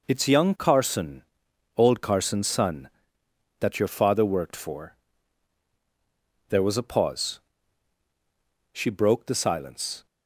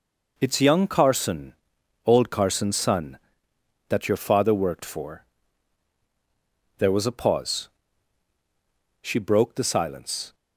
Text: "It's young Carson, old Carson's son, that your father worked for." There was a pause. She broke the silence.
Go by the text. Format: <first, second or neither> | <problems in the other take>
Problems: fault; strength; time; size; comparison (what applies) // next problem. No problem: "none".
neither | none